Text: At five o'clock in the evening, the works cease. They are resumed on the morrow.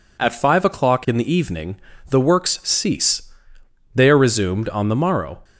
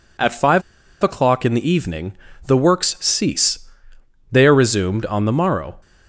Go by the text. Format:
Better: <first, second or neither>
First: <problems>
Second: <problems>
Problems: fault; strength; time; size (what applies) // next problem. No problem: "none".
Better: first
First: none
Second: pauses between "five" and "o'clock"; at 0.6 s; 0.40 s long